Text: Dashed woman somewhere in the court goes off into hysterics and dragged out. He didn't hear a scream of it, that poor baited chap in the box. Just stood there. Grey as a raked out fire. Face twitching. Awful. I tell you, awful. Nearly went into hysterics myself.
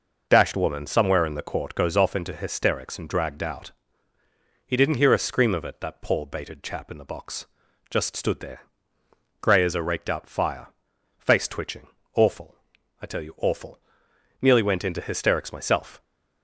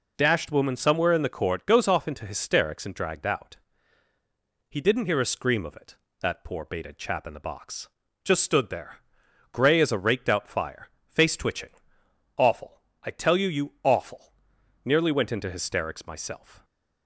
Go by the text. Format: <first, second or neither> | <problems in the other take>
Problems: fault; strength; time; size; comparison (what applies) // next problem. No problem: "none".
first | says "you" twice; at 13.4 s